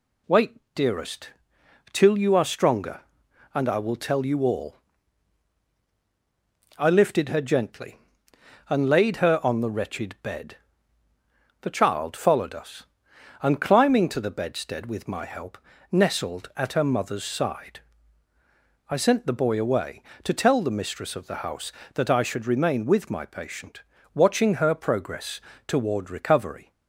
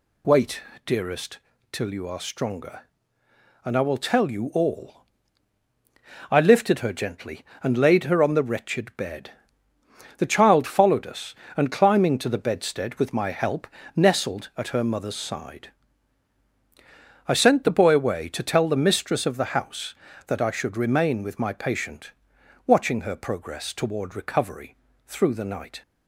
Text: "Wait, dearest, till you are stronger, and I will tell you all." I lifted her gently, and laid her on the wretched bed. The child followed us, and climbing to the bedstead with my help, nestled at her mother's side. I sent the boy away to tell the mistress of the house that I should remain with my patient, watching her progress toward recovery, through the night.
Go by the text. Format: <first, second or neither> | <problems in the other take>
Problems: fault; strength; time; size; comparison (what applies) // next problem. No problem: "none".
second | pauses between "progress" and "toward"; slight; at 25.4 s; 0.24 s long // stops before "through the night"; at 26.7 s